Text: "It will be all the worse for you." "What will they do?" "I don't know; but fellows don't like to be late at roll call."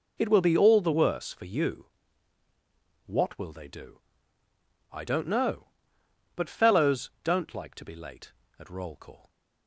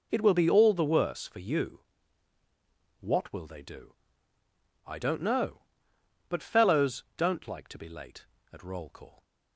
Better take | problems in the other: neither | none

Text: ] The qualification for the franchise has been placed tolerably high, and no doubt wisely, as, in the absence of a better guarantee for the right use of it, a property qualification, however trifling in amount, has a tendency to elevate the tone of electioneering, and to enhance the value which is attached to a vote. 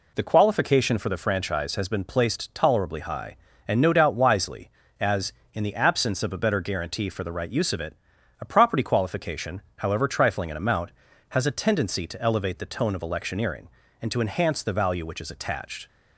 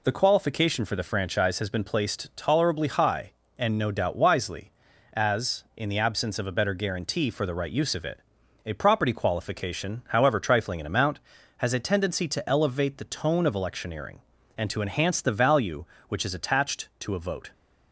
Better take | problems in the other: second | stops before "to a vote"; at 15.8 s

